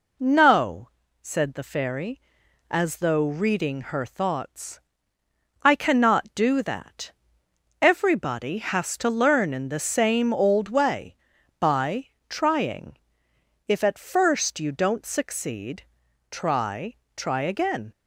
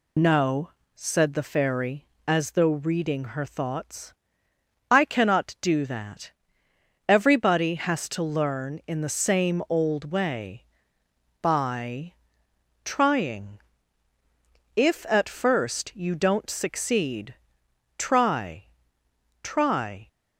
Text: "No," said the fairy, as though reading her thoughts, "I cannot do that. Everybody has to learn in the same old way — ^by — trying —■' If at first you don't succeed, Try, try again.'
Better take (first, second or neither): first